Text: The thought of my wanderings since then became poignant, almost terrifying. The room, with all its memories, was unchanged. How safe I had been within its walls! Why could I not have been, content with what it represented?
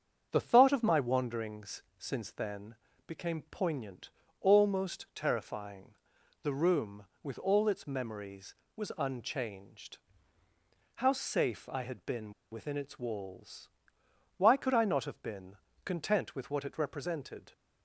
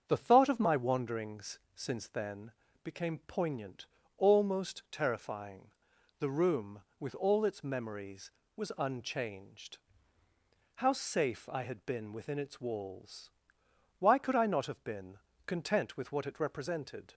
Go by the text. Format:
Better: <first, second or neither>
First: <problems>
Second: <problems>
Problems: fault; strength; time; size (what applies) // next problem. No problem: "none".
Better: second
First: starts louder than the rest; until 1.3 s; 7 dB // pauses between "then" and "became"; slight; at 2.7 s; 0.32 s long // pauses between "been" and "within"; slight; at 12.3 s; 0.18 s long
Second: starts louder than the rest; until 1.0 s; 7 dB // pauses between "then" and "became"; slight; at 2.5 s; 0.32 s long